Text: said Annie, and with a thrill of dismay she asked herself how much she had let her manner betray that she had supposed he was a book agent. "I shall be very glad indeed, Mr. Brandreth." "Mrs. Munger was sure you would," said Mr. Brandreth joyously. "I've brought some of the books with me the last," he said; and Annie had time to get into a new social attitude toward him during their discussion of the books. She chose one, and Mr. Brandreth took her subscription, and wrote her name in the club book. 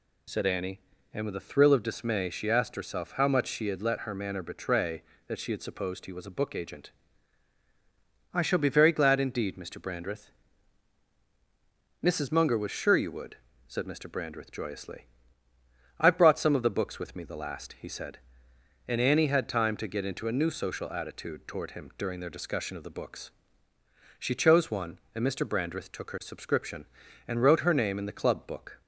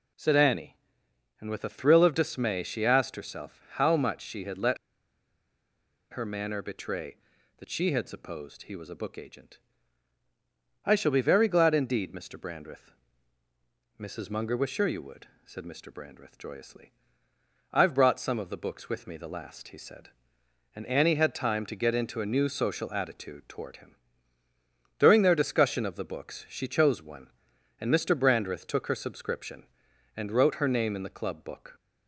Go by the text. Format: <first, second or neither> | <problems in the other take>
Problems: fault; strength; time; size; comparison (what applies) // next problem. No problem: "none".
first | pauses between "let" and "her"; strong; at 4.7 s; 1.3 s long // pauses between "him" and "during"; at 23.9 s; 1.0 s long